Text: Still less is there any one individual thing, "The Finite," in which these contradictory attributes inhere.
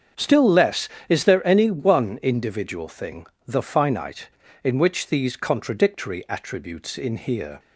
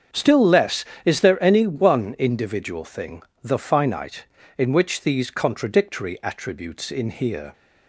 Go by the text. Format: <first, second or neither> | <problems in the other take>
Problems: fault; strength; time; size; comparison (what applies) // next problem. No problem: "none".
neither | starts louder than the rest; strong; the same in both